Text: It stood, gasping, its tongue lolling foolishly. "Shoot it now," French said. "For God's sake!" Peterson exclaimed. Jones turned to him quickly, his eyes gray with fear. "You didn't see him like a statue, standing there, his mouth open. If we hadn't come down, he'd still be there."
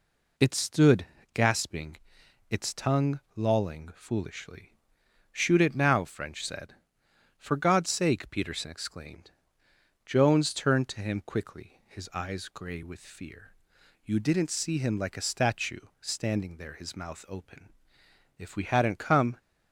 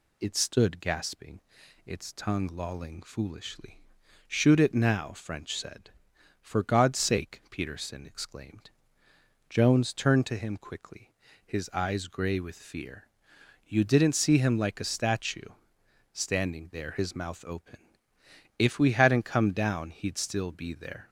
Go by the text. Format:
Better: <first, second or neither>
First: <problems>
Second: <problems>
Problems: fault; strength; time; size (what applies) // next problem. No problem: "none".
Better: second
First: stops before "down he'd still be there"; at 19.3 s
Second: none